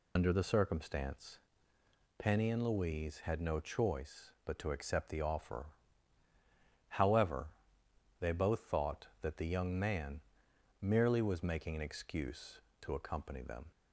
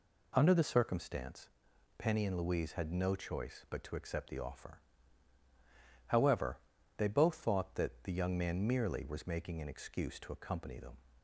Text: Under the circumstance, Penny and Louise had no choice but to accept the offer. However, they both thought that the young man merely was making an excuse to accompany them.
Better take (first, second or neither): second